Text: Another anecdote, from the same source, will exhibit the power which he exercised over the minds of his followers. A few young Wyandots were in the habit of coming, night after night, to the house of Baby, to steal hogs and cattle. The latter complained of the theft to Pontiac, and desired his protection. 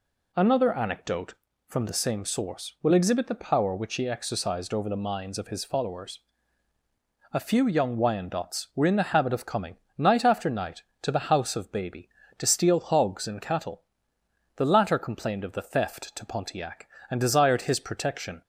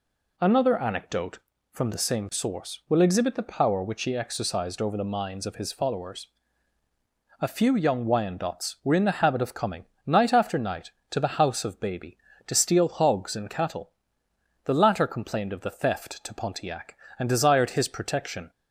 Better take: neither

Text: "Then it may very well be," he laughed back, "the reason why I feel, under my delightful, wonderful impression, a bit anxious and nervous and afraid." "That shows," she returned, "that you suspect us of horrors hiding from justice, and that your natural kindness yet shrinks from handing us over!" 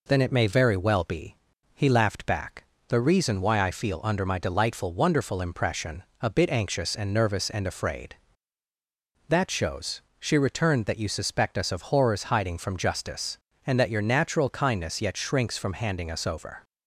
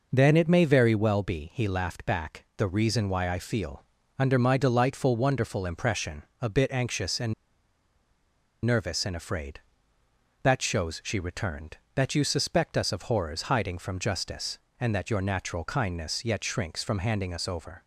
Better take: first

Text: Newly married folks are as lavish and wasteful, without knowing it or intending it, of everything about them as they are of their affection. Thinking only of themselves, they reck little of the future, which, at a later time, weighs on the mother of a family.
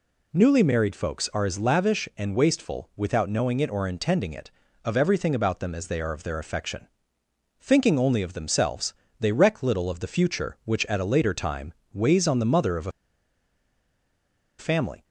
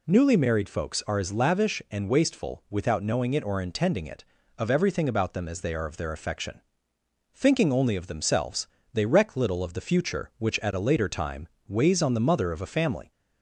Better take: second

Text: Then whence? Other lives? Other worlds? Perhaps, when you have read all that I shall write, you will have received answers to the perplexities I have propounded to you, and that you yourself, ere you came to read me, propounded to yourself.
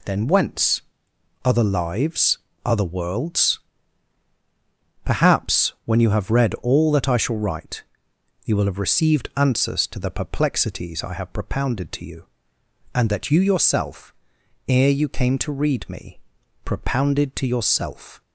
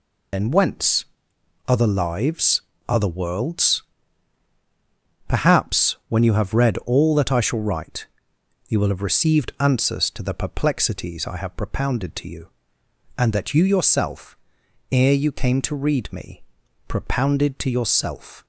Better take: first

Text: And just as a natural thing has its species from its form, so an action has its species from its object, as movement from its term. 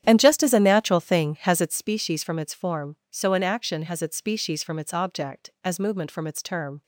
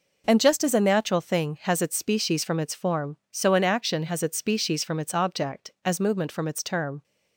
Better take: second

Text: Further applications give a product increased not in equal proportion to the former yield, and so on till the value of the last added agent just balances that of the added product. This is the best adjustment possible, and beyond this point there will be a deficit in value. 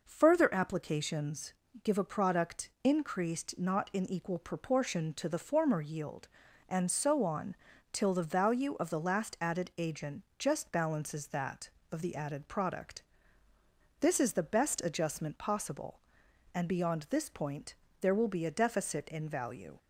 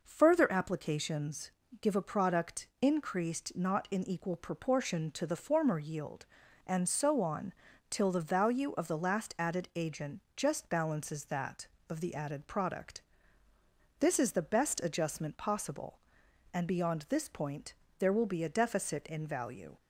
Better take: neither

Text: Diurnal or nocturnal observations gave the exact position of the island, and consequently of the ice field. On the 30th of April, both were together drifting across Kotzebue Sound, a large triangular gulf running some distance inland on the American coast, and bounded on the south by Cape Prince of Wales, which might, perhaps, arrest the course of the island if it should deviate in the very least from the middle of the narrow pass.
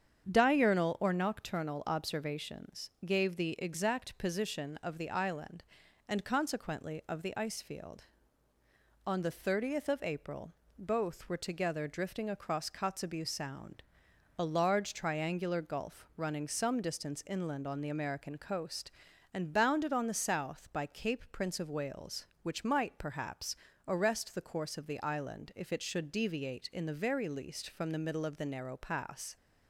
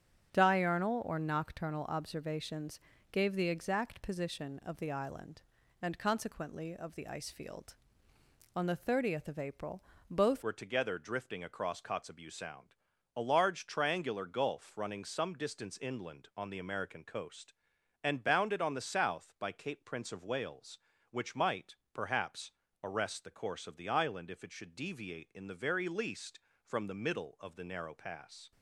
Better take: first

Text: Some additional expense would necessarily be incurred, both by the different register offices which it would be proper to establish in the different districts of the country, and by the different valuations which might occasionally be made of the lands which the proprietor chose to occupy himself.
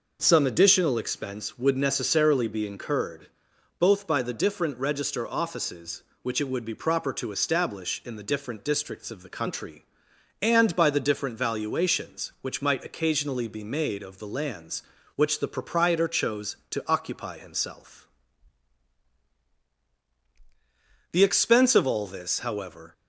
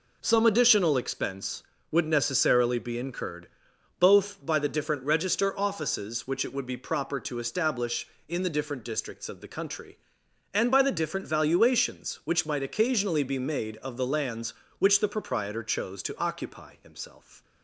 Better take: second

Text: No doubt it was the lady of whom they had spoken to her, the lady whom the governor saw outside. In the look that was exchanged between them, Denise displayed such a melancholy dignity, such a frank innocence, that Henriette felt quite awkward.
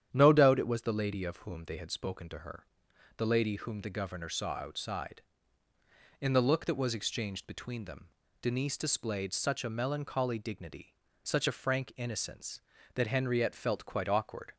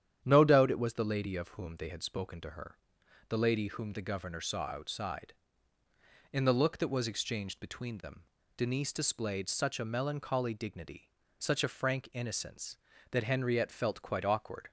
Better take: neither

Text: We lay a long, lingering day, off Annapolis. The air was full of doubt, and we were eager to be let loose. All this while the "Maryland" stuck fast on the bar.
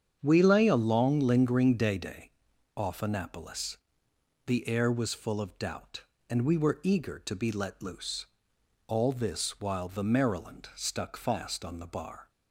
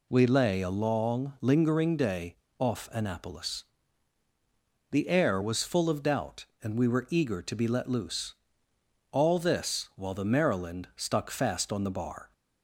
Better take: second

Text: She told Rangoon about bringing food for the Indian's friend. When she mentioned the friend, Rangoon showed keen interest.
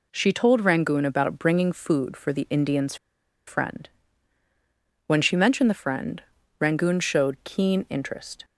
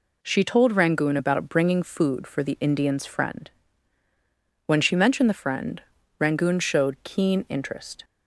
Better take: second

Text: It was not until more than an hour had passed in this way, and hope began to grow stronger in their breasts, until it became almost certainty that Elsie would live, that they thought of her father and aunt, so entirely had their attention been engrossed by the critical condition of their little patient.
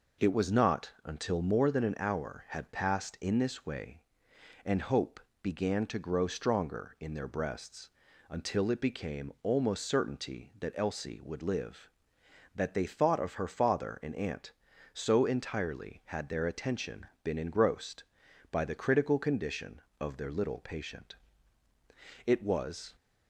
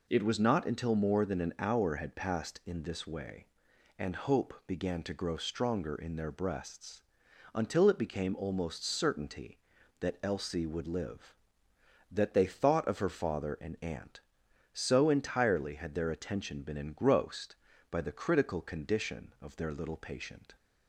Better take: second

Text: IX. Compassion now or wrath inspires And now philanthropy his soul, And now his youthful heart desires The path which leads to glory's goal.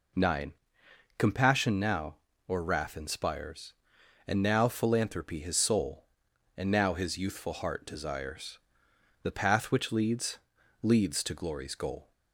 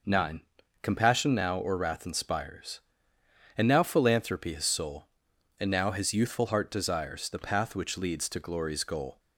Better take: second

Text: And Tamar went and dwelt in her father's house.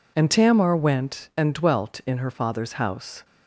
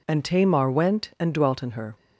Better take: first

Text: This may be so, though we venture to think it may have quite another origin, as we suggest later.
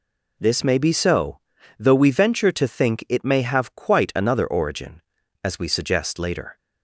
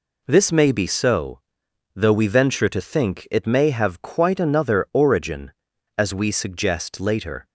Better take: neither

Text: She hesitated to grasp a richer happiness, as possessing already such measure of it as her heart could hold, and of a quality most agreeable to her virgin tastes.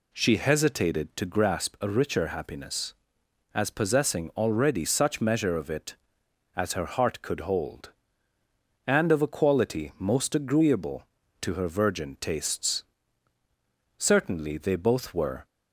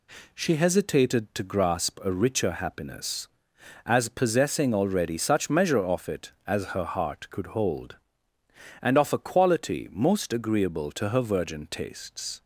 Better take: second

